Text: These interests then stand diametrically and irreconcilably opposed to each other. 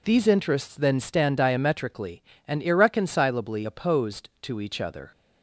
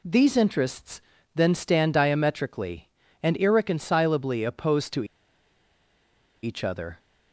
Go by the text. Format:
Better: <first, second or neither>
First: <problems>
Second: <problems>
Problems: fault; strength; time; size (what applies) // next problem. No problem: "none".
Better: first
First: none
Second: pauses between "interests" and "then"; slight; at 1.0 s; 0.32 s long // pauses between "to" and "each"; strong; at 5.0 s; 1.3 s long